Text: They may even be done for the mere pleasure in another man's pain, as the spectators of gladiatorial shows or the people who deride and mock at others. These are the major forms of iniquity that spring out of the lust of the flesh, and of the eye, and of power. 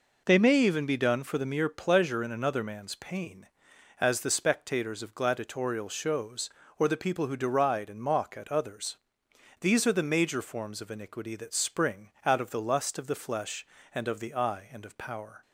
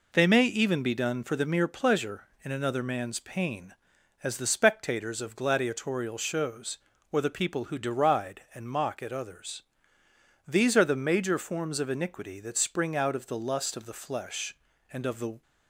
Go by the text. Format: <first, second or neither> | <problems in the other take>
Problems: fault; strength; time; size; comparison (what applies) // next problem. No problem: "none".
first | stops before "eye and of power"; at 15.4 s